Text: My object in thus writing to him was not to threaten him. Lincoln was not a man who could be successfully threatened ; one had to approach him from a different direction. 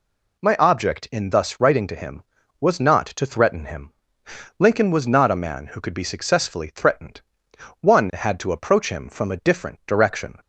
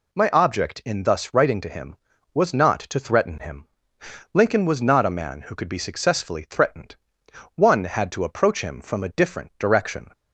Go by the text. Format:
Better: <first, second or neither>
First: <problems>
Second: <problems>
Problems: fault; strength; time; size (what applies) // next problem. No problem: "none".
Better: neither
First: none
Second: none